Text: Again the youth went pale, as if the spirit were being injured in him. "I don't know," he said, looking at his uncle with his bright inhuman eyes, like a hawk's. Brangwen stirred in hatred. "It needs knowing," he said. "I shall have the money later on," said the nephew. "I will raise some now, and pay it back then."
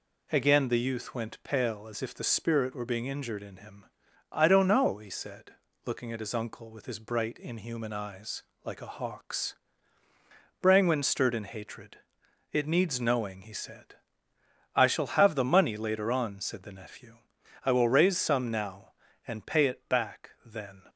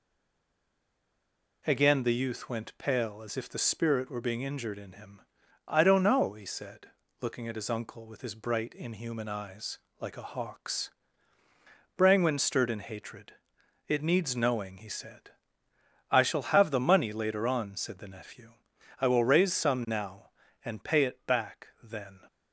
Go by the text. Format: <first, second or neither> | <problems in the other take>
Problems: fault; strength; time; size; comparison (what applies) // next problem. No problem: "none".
first | stays silent before the first word; noticeable; until 1.6 s; 1.6 s long